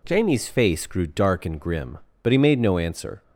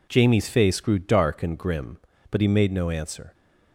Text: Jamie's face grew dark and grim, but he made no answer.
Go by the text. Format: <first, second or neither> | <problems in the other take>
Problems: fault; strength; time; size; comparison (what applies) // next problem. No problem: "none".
neither | none